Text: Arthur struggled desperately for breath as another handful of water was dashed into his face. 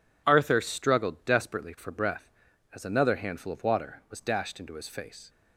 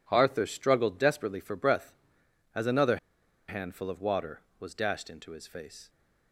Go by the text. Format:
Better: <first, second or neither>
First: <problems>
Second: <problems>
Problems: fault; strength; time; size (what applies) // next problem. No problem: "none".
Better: first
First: none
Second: pauses between "another" and "handful"; noticeable; at 2.9 s; 0.50 s long